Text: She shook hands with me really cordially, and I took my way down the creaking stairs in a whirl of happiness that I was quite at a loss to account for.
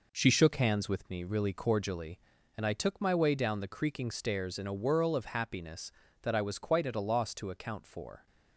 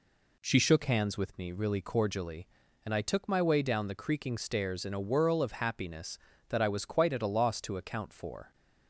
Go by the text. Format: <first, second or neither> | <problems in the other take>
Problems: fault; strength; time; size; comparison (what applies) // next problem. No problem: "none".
second | gets quieter; noticeable; throughout; 6 dB